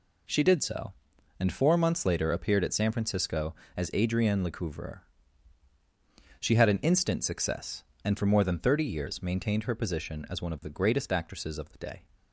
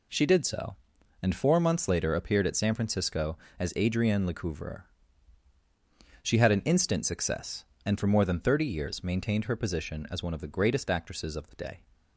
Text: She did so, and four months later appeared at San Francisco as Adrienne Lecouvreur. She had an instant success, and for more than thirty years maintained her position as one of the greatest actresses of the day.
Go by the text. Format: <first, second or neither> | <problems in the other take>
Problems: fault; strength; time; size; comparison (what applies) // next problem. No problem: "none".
neither | none